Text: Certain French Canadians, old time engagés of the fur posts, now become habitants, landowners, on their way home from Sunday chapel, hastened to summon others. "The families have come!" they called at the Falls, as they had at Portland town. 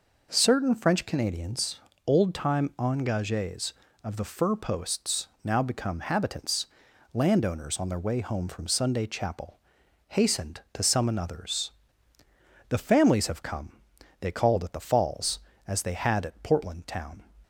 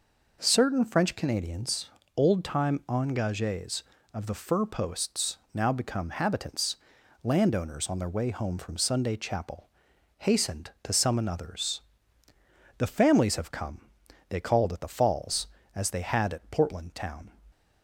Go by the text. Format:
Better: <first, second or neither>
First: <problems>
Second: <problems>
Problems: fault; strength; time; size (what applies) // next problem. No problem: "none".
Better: neither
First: none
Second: none